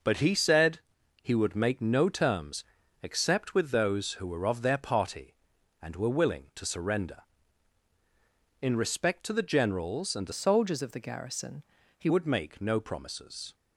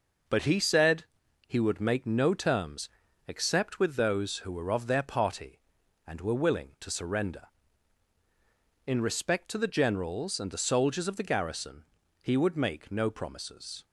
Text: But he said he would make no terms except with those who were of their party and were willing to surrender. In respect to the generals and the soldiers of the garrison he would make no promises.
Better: second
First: pauses between "said" and "he"; at 0.7 s; 0.42 s long // pauses between "terms" and "except"; at 2.6 s; 0.38 s long // changes voice from "soldiers" to "he"; from 10.3 to 12.0 s; 1.7 s long // pauses between "garrison" and "he"; slight; at 11.6 s; 0.34 s long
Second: pauses between "said" and "he"; at 1.0 s; 0.42 s long // pauses between "terms" and "except"; at 2.8 s; 0.38 s long // pauses between "garrison" and "he"; at 11.8 s; 0.38 s long

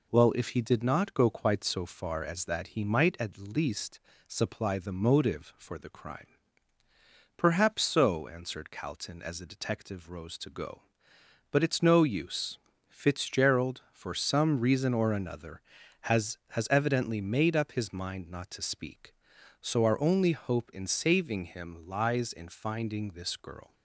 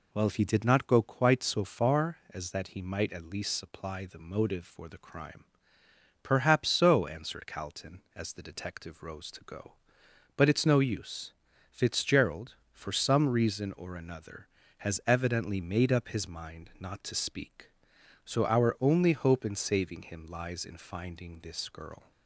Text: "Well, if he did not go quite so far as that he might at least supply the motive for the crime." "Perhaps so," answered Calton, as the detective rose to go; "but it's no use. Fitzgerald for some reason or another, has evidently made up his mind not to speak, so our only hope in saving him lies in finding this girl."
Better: second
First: pauses between "least" and "supply"; slight; at 3.9 s; 0.26 s long // says "has" twice; at 16.5 s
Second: none

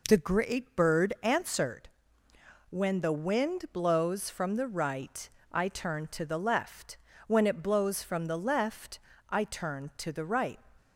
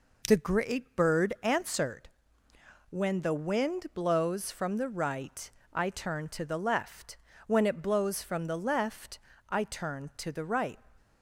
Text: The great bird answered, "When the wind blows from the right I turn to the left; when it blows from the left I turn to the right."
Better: neither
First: pauses between "right" and "I"; slight; at 5.2 s; 0.24 s long // pauses between "left" and "I"; slight; at 8.9 s; 0.30 s long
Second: pauses between "right" and "I"; slight; at 5.4 s; 0.24 s long // pauses between "left" and "I"; slight; at 9.1 s; 0.30 s long

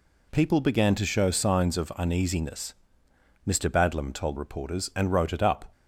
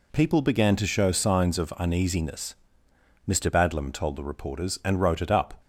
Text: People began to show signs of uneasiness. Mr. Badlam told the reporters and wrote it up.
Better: second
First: skips "the"; at 4.3 s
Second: none

